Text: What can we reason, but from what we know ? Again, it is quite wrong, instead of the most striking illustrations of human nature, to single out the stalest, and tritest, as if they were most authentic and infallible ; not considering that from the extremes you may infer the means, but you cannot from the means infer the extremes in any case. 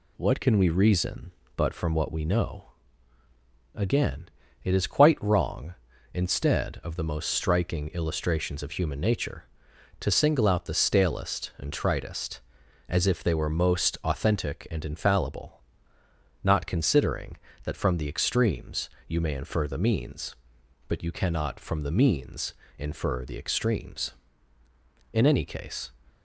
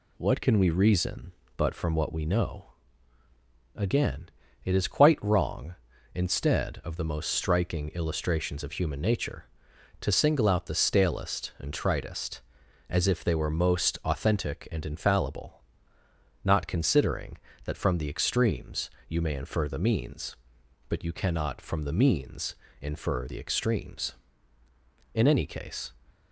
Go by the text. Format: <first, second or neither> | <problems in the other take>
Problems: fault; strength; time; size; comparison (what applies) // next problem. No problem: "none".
neither | pauses between "extremes" and "you"; slight; the same in both // pauses between "means" and "infer"; slight; the same in both